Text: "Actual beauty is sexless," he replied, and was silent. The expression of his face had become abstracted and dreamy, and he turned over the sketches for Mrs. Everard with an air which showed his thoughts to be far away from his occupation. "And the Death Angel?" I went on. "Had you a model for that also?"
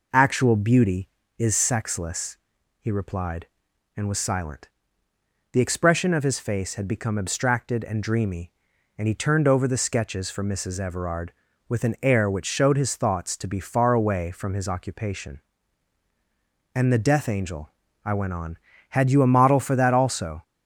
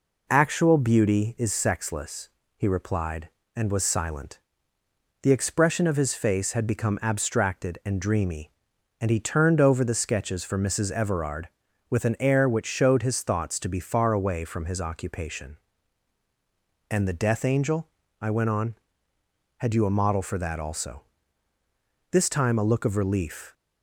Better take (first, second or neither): first